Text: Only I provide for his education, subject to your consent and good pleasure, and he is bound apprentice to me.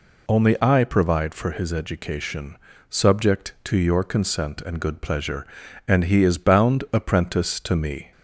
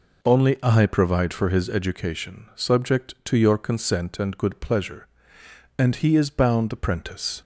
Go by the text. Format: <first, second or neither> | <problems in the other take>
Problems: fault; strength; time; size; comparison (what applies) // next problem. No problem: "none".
first | stops before "to me"; at 7.4 s